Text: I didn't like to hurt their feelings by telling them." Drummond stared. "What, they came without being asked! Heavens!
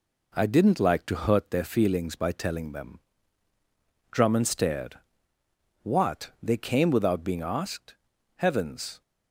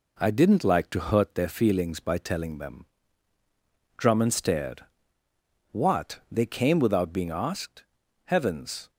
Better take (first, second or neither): neither